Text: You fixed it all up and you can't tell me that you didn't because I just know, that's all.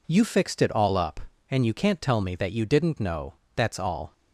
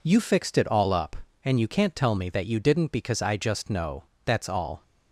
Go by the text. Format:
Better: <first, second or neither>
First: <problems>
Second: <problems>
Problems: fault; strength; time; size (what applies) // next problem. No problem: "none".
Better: second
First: skips "because I just"; at 2.9 s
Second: none